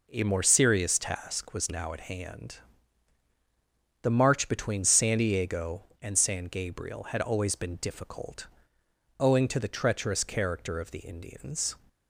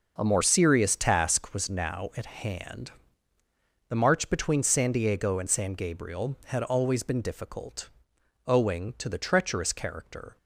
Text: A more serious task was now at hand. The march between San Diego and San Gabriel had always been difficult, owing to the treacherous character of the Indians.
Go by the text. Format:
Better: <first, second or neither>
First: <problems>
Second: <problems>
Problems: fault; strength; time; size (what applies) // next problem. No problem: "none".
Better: first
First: none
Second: starts louder than the rest; noticeable; until 1.1 s; 6 dB // stops before "of the Indians"; at 10.3 s